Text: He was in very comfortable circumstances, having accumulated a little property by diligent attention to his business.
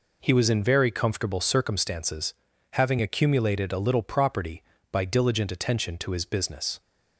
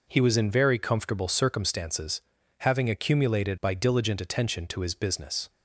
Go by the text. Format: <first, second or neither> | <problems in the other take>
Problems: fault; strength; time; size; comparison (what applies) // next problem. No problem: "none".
first | skips "a little property"; at 3.5 s